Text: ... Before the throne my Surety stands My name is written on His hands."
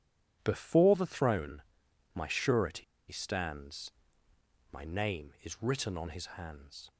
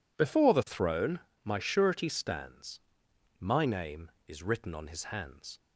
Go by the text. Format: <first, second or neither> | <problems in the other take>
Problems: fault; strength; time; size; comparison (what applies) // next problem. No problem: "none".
second | pauses between "throne" and "my"; noticeable; at 1.6 s; 0.50 s long; slight in the second // pauses between "Surety" and "stands"; slight; at 2.8 s; 0.26 s long // pauses between "stands" and "My"; noticeable; at 3.9 s; 0.80 s long; noticeable in the second